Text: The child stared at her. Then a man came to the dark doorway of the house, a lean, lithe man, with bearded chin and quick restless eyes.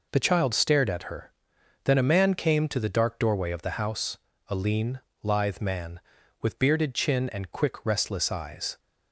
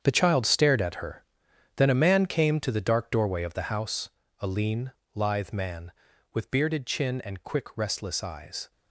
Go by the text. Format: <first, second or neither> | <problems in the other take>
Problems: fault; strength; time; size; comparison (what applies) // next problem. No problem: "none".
first | gets quieter; strong; throughout; 13 dB